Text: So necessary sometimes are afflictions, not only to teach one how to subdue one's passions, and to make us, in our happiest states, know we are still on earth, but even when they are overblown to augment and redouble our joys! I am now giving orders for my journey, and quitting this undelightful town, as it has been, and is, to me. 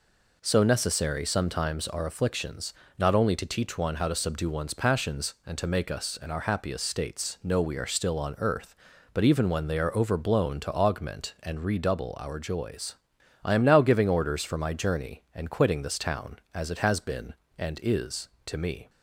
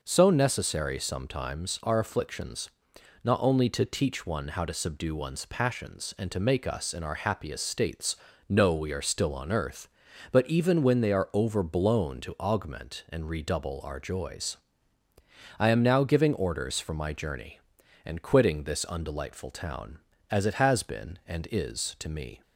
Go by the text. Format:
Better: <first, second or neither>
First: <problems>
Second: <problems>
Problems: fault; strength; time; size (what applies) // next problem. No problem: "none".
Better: second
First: skips "undelightful"; at 15.9 s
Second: none